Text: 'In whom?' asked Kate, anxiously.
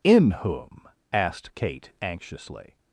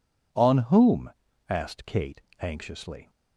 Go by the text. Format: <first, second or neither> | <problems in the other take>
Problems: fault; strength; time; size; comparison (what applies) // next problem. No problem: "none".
first | says "On" for "In"; at 0.3 s